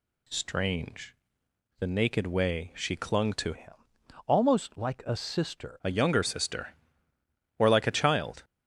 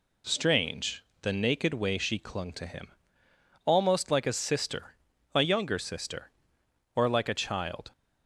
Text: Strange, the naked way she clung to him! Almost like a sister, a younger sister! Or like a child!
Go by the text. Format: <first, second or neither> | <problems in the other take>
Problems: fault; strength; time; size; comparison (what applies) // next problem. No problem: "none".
second | changes voice from "him" to "sister"; from 3.5 to 5.7 s; 2.2 s long